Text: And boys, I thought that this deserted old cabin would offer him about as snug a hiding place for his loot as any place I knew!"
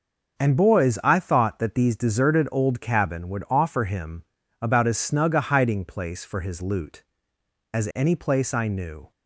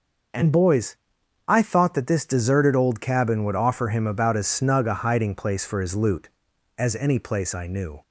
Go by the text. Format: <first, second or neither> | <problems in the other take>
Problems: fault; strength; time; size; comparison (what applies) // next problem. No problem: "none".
second | starts louder than the rest; until 1.4 s; 6 dB; also in the second // says "these" for "this"; at 1.7 s // pauses between "him" and "about"; slight; at 4.2 s; 0.36 s long